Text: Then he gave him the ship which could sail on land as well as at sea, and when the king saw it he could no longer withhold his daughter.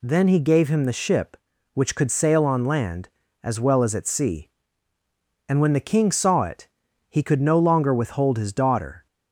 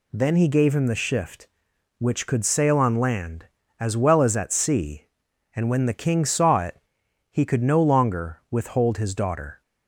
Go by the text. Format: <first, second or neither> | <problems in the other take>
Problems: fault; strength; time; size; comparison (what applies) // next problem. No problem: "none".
first | says "shift" for "ship"; at 0.9 s // pauses between "it" and "he"; noticeable; at 6.7 s; 0.50 s long; also in the first